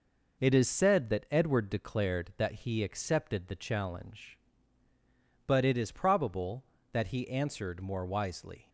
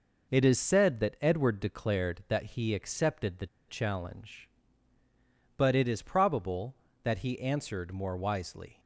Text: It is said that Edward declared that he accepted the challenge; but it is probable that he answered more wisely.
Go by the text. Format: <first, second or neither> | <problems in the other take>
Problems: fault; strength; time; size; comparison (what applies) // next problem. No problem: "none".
first | pauses between "the" and "challenge"; slight; at 3.4 s; 0.22 s long